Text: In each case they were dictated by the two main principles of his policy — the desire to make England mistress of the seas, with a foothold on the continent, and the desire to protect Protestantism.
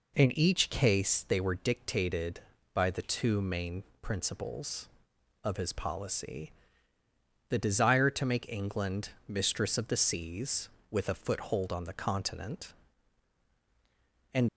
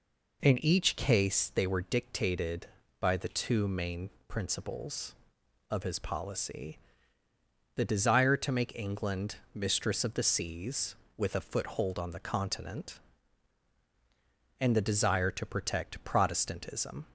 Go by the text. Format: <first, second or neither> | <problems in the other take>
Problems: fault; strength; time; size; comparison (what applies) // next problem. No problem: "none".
second | pauses between "main" and "principles"; slight; at 3.8 s; 0.18 s long; slight in the second // pauses between "England" and "mistress"; slight; at 9.0 s; 0.18 s long; slight in the second // stops before "the desire to protect Protestantism"; at 14.4 s